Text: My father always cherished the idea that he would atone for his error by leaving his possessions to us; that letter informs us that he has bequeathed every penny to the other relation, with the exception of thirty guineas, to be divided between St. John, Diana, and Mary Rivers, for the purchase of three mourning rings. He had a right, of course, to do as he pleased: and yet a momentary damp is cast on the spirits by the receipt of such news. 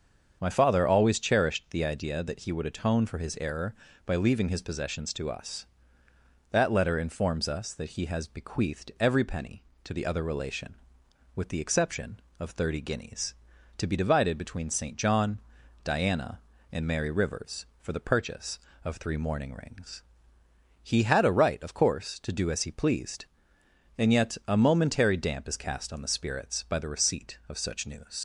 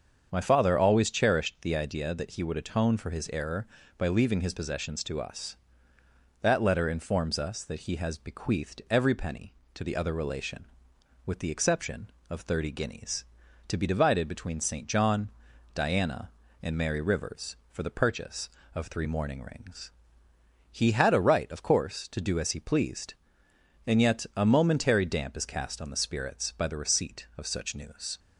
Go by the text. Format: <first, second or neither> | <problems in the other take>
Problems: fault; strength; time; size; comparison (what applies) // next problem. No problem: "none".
second | starts louder than the rest; strong; until 1.4 s; 7 dB; strong in the second // leaves "news" unfinished; at 28.1 s; 65 ms